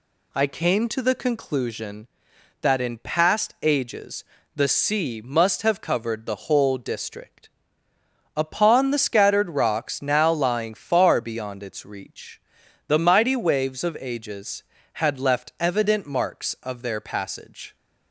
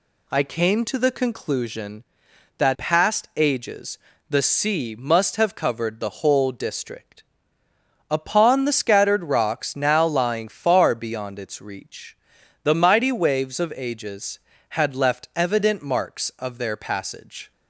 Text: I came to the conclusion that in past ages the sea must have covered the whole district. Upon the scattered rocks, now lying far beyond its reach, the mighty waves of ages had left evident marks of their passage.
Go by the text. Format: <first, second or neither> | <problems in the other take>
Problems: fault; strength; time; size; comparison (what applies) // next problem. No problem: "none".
first | skips "in"; at 2.7 s // pauses between "ages" and "the"; slight; at 3.9 s; 0.32 s long; slight in the first